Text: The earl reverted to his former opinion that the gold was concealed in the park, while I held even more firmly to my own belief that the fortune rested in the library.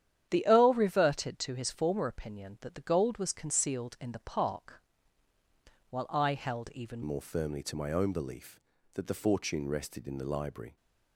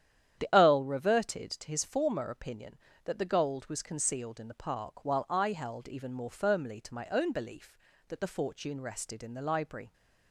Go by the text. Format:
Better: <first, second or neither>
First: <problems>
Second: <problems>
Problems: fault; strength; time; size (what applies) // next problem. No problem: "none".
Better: second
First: starts louder than the rest; strong; until 1.3 s; 10 dB // changes voice at "more"; from 7.0 s on; 3.7 s long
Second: starts louder than the rest; strong; until 1.4 s; 10 dB